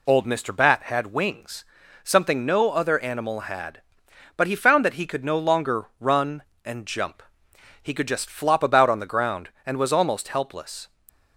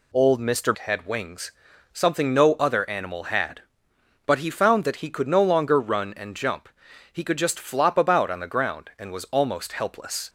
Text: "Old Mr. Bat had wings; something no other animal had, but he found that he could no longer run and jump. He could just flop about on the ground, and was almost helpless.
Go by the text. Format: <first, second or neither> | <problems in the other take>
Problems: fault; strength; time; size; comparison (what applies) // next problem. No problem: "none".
first | skips "Bat"; at 0.7 s